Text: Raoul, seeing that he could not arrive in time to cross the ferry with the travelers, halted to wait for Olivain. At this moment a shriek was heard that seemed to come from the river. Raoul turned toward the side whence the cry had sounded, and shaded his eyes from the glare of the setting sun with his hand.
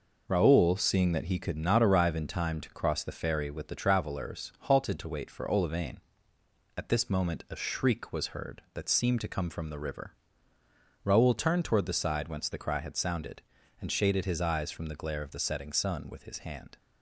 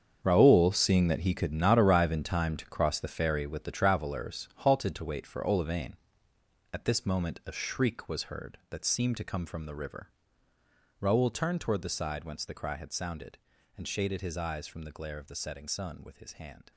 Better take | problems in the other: first | gets quieter; strong; throughout; 13.5 dB

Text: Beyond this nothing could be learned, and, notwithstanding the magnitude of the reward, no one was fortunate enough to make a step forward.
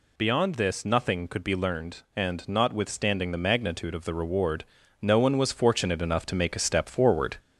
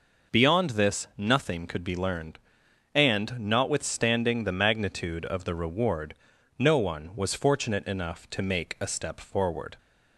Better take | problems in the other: second | gets louder; slight; throughout; 2.5 dB

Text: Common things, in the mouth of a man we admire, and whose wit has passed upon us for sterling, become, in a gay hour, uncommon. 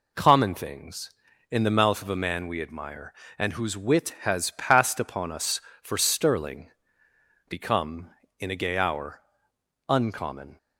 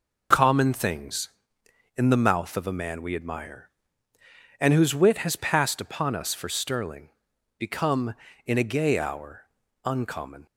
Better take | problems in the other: neither | none

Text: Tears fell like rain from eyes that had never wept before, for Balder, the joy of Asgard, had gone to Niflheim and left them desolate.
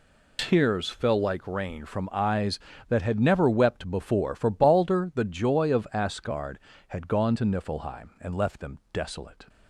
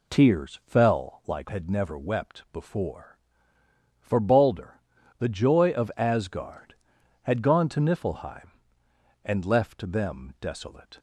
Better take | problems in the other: first | skips "rain from eyes that"; at 1.4 s

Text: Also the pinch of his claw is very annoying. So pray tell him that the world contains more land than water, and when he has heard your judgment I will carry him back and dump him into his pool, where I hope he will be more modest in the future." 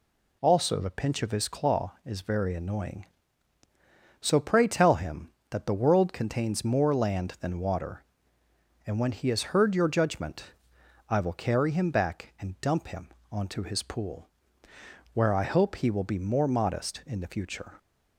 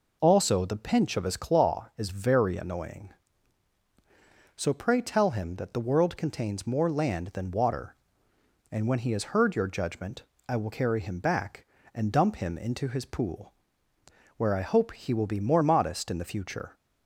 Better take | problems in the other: second | pauses between "judgment" and "I"; noticeable; at 10.5 s; 0.56 s long; slight in the second // says "onto" for "into"; at 13.3 s

